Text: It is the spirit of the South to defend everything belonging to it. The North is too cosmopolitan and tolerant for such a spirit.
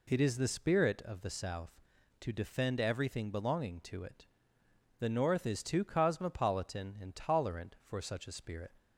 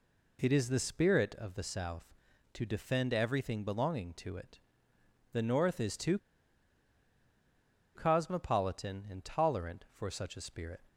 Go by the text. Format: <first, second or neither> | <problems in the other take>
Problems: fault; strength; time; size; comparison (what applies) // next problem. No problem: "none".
first | pauses between "too" and "cosmopolitan"; strong; at 6.1 s; 1.7 s long